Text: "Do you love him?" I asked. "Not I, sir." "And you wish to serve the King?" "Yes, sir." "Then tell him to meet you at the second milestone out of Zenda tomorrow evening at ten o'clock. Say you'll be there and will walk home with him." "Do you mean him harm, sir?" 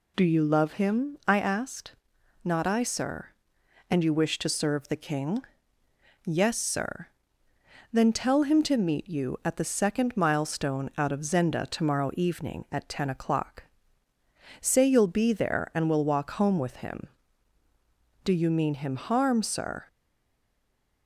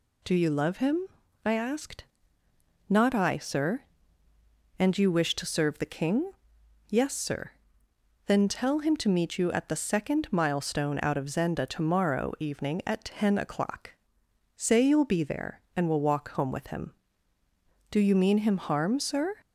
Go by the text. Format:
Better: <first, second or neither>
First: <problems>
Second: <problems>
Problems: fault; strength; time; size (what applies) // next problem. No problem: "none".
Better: second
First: stays silent after the last word; noticeable; from 19.8 s on; 1.2 s long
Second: none